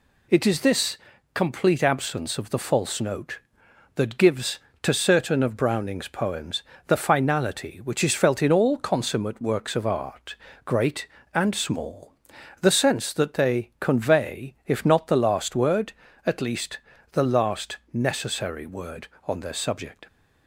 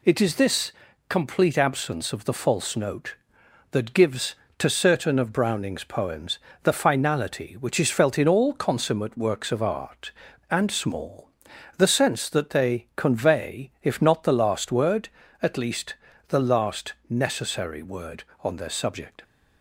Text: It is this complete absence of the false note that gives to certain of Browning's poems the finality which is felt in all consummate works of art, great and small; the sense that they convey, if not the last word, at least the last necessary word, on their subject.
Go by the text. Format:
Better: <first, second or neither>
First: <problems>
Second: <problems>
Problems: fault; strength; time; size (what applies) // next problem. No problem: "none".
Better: first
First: pauses between "this" and "complete"; slight; at 0.9 s; 0.34 s long // pauses between "poems" and "the"; slight; at 6.6 s; 0.26 s long // pauses between "least" and "the"; slight; at 16.7 s; 0.34 s long // pauses between "last" and "necessary"; slight; at 17.7 s; 0.16 s long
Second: pauses between "this" and "complete"; slight; at 0.7 s; 0.34 s long // pauses between "poems" and "the"; slight; at 6.3 s; 0.26 s long // skips "great"; at 10.2 s // pauses between "least" and "the"; slight; at 15.9 s; 0.34 s long // pauses between "last" and "necessary"; slight; at 16.9 s; 0.16 s long